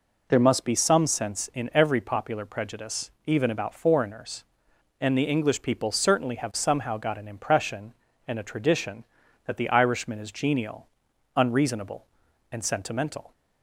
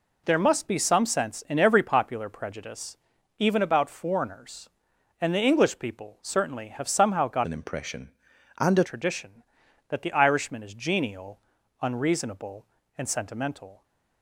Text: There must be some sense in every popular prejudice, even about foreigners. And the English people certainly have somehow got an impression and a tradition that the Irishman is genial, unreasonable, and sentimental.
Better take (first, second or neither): first